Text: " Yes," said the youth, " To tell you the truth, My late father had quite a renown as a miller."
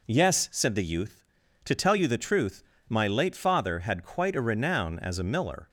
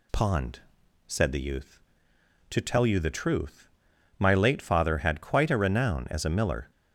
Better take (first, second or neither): first